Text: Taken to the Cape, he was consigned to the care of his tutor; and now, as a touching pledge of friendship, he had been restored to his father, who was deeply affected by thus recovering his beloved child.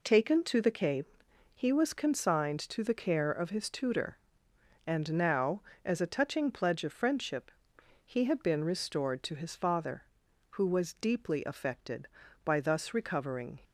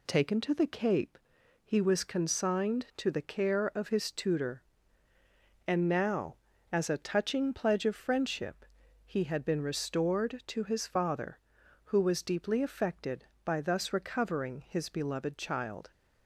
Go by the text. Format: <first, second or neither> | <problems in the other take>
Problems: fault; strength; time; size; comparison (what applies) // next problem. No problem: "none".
second | stops before "his beloved child"; at 13.6 s